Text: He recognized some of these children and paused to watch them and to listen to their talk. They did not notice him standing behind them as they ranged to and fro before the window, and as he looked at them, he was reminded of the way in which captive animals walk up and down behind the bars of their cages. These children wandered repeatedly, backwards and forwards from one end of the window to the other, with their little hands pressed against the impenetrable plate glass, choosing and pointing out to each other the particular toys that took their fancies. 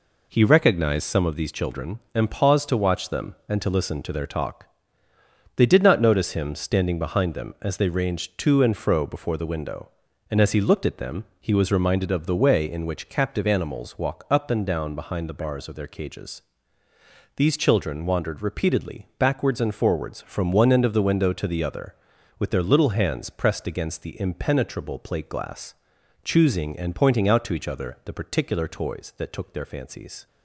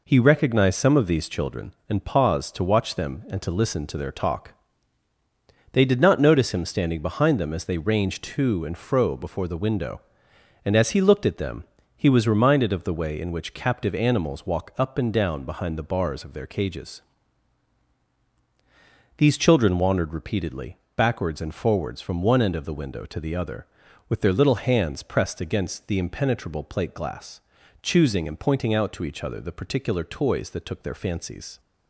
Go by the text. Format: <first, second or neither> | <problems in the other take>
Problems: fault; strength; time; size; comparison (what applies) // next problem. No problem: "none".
neither | none